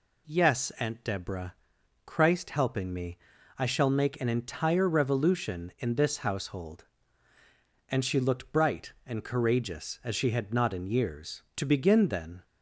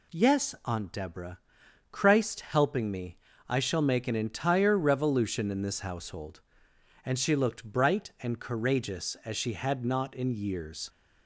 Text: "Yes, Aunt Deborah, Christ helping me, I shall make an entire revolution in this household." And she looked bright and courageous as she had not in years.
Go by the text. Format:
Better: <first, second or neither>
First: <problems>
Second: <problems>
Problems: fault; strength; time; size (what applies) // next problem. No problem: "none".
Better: second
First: goes on to say "To begin then"; noticeable; from 11.5 s on; 0.86 s long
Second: none